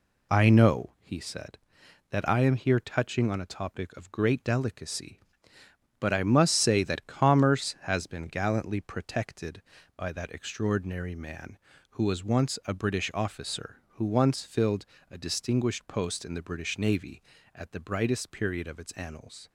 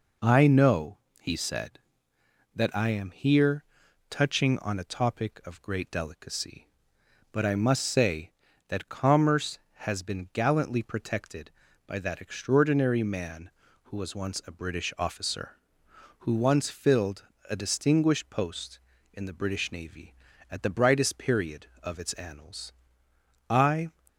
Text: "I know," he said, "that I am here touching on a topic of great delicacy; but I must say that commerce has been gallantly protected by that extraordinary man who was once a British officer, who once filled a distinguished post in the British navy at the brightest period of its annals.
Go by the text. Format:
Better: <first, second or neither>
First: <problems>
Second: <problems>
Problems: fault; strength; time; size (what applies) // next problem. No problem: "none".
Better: first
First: pauses between "filled" and "a"; slight; at 14.8 s; 0.24 s long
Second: pauses between "here" and "touching"; at 3.6 s; 0.44 s long // pauses between "filled" and "a"; slight; at 17.2 s; 0.22 s long // goes on to say "I"; slight; from 23.5 s on; 0.40 s long